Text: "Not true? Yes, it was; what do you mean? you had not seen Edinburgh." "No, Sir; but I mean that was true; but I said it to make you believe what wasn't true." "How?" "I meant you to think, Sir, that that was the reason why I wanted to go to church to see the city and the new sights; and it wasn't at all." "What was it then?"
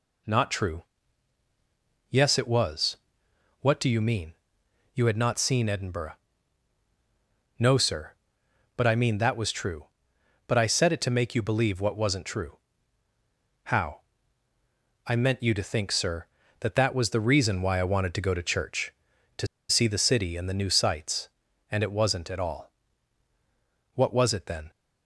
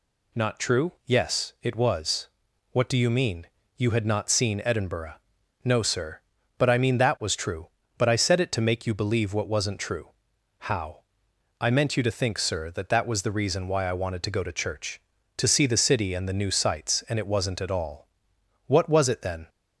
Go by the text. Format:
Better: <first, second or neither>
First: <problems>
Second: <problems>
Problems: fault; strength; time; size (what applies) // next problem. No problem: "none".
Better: second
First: pauses between "to" and "see"; slight; at 19.4 s; 0.23 s long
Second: none